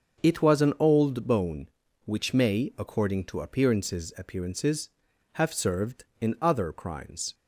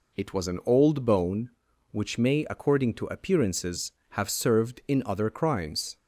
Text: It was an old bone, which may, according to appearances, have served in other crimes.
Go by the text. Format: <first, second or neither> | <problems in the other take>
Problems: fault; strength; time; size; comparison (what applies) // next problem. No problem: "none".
second | starts louder than the rest; until 1.2 s; 6.5 dB // says "appearances" twice; at 4.1 s